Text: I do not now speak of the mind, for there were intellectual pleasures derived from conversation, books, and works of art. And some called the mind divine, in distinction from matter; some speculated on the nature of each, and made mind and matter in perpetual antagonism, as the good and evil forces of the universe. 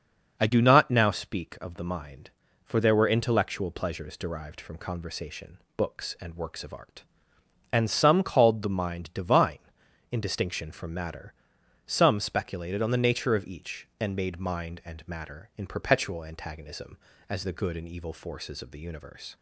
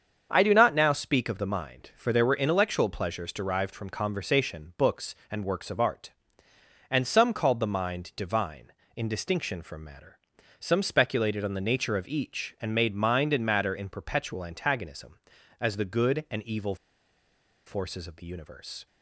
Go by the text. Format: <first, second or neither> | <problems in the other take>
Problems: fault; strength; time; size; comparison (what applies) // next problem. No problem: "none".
first | starts louder than the rest; strong; until 1.3 s; 7 dB; noticeable in the first // pauses between "evil" and "forces"; noticeable; at 16.7 s; 0.91 s long